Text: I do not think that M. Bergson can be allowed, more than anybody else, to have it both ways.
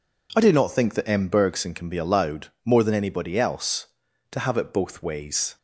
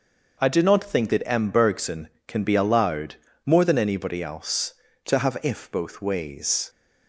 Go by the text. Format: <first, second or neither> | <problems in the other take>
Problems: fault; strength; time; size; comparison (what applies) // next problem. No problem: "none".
first | starts louder than the rest; noticeable; until 1.4 s; 6 dB // says "if" for "it"; at 5.4 s